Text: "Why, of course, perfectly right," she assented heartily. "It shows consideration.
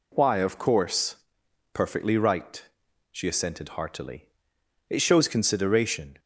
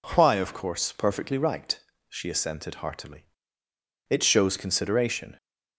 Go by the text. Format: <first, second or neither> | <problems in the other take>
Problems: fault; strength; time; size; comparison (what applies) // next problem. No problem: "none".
neither | none